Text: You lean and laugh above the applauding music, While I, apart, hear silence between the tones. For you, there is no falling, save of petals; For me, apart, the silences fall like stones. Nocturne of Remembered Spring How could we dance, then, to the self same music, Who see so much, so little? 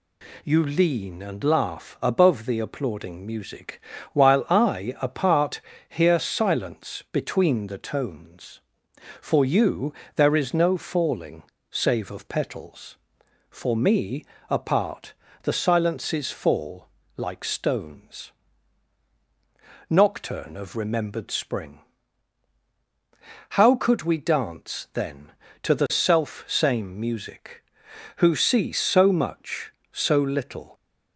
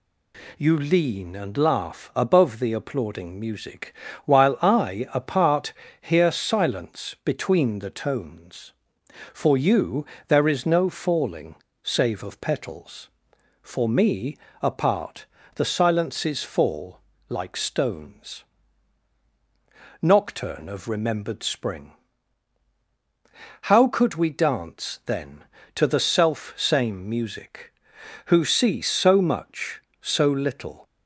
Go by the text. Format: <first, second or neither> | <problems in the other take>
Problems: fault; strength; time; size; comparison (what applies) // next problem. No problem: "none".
neither | pauses between "fall" and "like"; slight; the same in both // pauses between "Spring" and "How"; strong; the same in both